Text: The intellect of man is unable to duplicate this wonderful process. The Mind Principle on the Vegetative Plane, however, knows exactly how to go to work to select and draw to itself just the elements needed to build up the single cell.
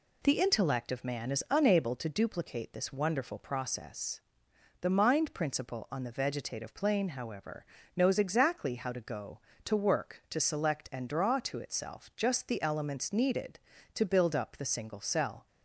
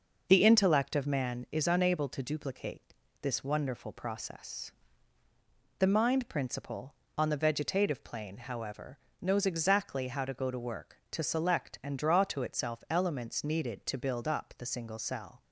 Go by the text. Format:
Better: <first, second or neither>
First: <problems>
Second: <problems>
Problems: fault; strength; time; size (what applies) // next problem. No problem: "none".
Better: first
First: none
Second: pauses between "duplicate" and "this"; slight; at 2.9 s; 0.28 s long // skips "just the"; at 12.8 s